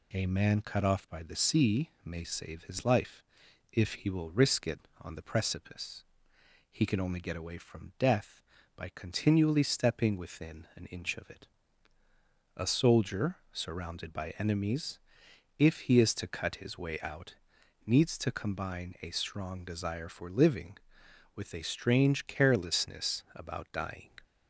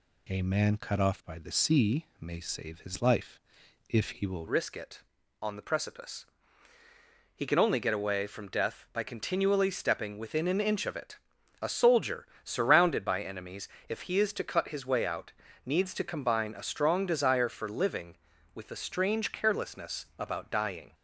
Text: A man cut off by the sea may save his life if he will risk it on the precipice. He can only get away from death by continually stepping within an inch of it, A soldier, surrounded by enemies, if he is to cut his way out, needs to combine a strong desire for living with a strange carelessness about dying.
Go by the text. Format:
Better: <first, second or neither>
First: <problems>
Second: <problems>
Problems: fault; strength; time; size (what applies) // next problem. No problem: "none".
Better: first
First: pauses between "life" and "if"; noticeable; at 3.2 s; 0.48 s long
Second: pauses between "life" and "if"; noticeable; at 3.3 s; 0.48 s long // changes voice at "risk"; from 4.4 s on; 16.5 s long